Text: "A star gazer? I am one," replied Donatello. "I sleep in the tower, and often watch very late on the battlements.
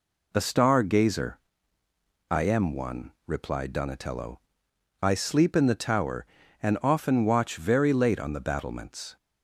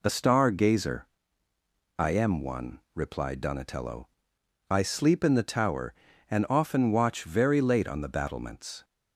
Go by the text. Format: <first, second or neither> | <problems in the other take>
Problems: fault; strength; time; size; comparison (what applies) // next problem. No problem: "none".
neither | none